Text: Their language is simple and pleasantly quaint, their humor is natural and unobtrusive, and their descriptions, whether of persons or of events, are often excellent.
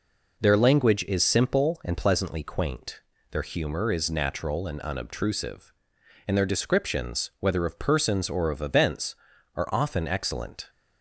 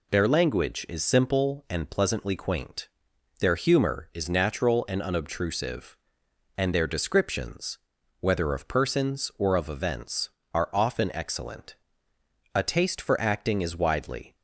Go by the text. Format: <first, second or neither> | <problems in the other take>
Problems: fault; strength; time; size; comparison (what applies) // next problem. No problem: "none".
first | goes on to say "A taste for acting is widely"; strong; from 12.5 s on; 1.8 s long